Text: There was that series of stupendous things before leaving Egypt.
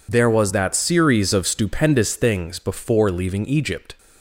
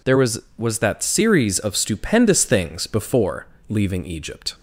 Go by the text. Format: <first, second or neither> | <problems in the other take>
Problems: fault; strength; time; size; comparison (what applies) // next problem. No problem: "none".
first | says "was" twice; at 0.5 s // pauses between "before" and "leaving"; slight; at 3.4 s; 0.20 s long